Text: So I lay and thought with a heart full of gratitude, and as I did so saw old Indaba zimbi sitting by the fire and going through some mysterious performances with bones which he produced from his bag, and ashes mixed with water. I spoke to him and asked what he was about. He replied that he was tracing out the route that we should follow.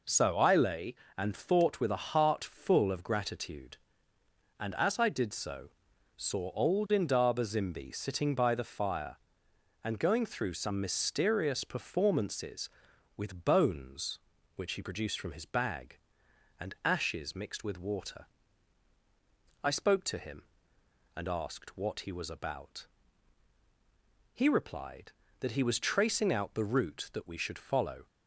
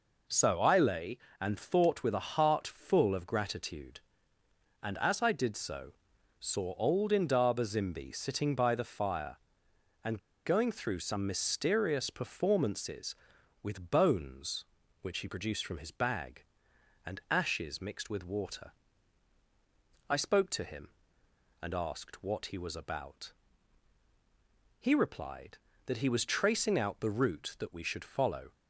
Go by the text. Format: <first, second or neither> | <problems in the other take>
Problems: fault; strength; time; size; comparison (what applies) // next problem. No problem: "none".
first | pauses between "so" and "saw"; noticeable; at 5.9 s; 0.46 s long; noticeable in the first // pauses between "and" and "going"; slight; at 10.1 s; 0.26 s long